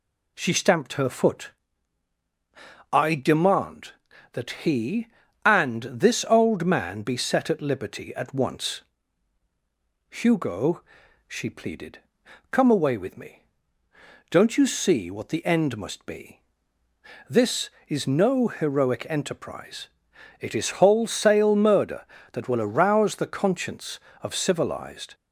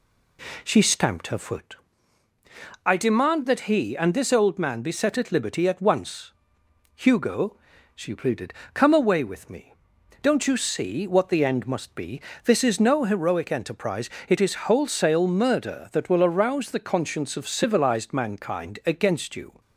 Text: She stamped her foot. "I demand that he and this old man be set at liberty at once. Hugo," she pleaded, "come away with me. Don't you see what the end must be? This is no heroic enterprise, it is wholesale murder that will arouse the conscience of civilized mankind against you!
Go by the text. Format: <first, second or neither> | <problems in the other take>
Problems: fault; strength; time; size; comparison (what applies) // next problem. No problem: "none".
second | stops before "mankind against you"; at 25.1 s